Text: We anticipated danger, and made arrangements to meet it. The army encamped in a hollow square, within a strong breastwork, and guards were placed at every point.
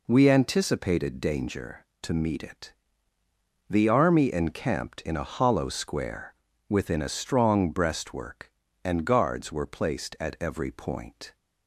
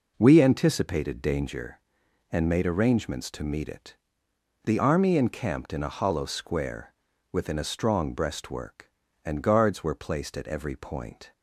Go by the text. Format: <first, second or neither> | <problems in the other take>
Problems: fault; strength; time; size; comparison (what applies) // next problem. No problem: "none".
second | skips "and made arrangements"; at 1.9 s